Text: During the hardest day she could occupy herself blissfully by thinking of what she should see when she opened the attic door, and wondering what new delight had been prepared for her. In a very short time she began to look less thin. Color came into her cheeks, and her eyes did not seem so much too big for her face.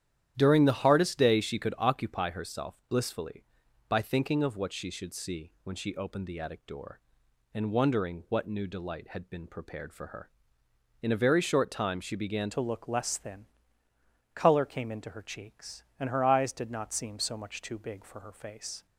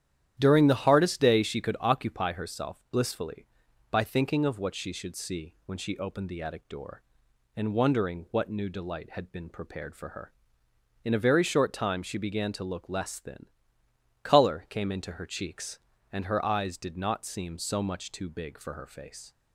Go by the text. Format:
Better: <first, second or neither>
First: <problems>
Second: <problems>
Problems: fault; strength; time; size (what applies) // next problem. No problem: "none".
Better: second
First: starts louder than the rest; strong; until 1.3 s; 10.5 dB // changes voice at "to"; from 12.5 s on; 6.3 s long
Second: starts louder than the rest; strong; until 1.3 s; 10.5 dB